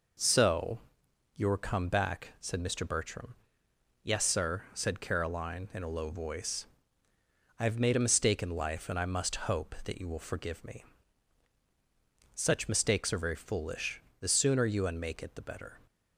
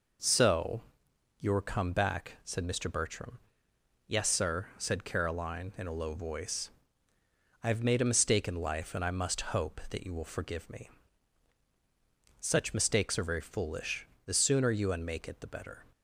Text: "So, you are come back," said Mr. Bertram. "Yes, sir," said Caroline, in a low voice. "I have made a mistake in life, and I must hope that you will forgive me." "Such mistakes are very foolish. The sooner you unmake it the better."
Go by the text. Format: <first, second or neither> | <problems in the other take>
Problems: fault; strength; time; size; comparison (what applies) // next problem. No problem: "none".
neither | none